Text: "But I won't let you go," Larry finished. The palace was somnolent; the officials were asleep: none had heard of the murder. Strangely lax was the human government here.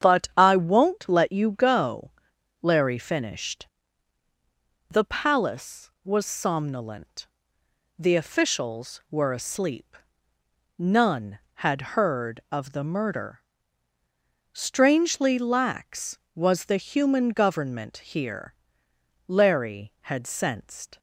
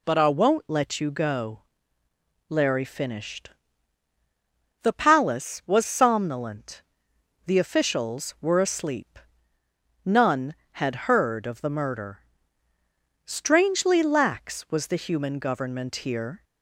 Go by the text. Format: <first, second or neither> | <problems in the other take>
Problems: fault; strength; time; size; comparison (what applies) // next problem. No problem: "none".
second | starts louder than the rest; strong; until 1.1 s; 8.5 dB // goes on to say "Larry had sensed"; strong; from 19.2 s on; 1.7 s long